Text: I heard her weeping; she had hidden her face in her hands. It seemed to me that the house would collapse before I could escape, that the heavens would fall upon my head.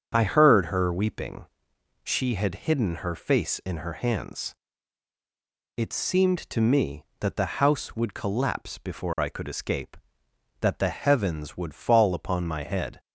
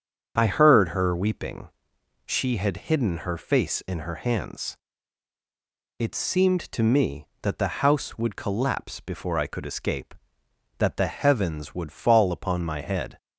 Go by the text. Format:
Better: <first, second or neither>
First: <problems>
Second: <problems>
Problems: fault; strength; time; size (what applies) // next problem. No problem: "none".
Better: neither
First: starts louder than the rest; strong; until 1.1 s; 7 dB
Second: starts louder than the rest; strong; until 1.3 s; 7 dB